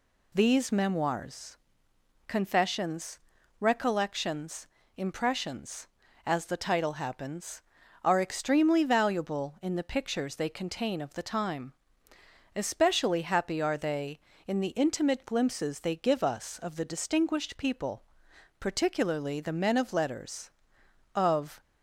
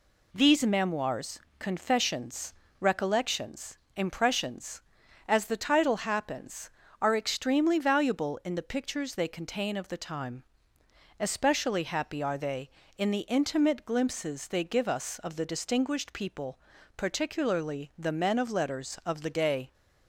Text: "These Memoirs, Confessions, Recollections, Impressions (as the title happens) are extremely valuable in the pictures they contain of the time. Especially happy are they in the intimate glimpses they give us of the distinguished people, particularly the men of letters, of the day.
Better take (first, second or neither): second